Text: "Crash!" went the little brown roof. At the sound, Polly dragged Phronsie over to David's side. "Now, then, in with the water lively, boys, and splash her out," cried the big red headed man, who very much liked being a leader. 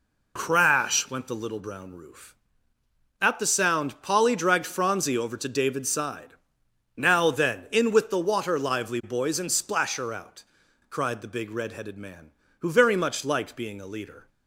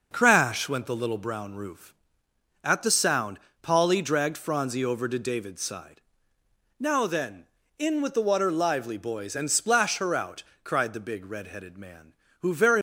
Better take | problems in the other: first | stops before "much liked being a leader"; at 12.7 s

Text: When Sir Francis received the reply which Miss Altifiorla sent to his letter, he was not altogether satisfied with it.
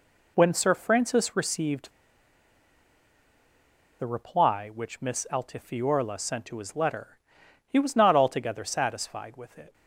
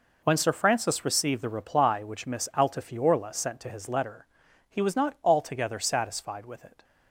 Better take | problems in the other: second | pauses between "received" and "the"; strong; at 1.9 s; 2.0 s long

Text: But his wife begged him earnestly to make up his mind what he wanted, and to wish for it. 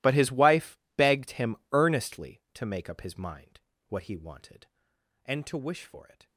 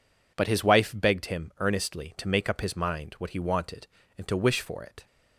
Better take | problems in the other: second | gets quieter; strong; throughout; 21.5 dB // pauses between "wife" and "begged"; slight; at 0.7 s; 0.20 s long // pauses between "him" and "earnestly"; slight; at 1.5 s; 0.16 s long // pauses between "mind" and "what"; slight; at 3.6 s; 0.28 s long

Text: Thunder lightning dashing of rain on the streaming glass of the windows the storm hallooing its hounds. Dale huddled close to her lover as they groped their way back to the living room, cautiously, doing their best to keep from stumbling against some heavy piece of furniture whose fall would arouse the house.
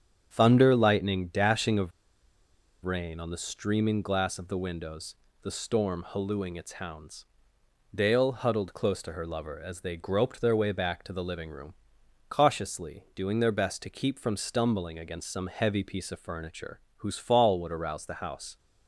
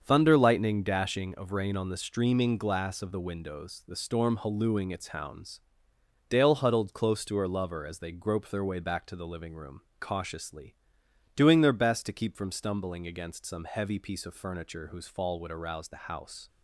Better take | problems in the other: second | starts louder than the rest; strong; until 1.3 s; 8 dB; also in the second // pauses between "of" and "rain"; noticeable; at 1.9 s; 0.92 s long // pauses between "windows" and "the"; slight; at 5.1 s; 0.26 s long // pauses between "furniture" and "whose"; slight; at 16.7 s; 0.18 s long

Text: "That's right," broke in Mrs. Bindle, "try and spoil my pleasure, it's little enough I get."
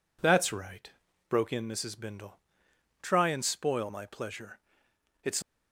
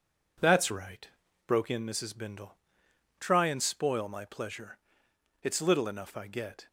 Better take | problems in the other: second | stops before "little enough I get"; at 5.4 s

